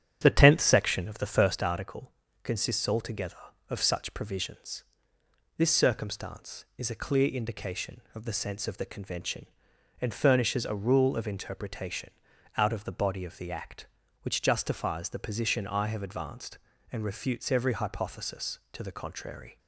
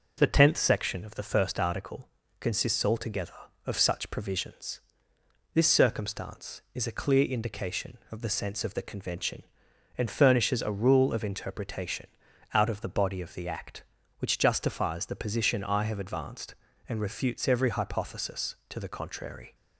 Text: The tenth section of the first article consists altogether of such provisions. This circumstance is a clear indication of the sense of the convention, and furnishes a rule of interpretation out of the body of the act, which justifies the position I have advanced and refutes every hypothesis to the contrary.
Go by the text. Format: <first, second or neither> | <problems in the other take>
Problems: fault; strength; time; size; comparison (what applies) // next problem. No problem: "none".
second | starts louder than the rest; strong; until 1.7 s; 9 dB // pauses between "article" and "consists"; slight; at 2.1 s; 0.32 s long; slight in the second // pauses between "interpretation" and "out"; noticeable; at 12.1 s; 0.46 s long; noticeable in the second